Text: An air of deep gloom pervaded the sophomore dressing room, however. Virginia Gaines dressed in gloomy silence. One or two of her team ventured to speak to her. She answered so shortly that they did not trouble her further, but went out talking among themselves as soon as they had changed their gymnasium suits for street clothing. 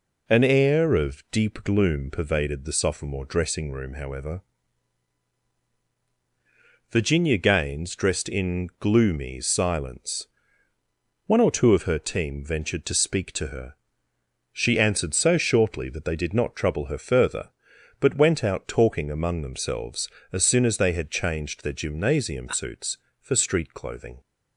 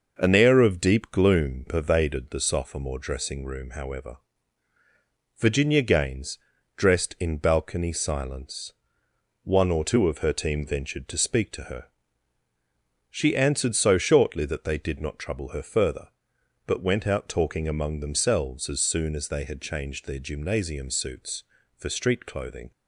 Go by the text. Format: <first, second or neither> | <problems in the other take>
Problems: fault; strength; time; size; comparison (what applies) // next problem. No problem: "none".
first | pauses between "Gaines" and "dressed"; slight; at 6.3 s; 0.36 s long // says "balcony" for "gloomy"; at 7.3 s